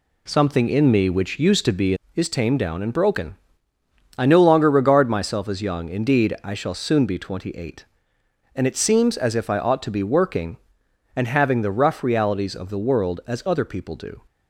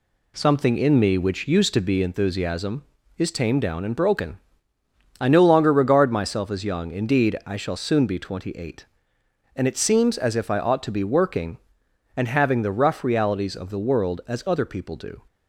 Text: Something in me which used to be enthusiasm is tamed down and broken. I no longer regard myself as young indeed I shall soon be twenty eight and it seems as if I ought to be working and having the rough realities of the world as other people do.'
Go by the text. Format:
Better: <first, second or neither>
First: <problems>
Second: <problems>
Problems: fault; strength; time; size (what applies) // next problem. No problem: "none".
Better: second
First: skips "enthusiasm"; at 2.0 s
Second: none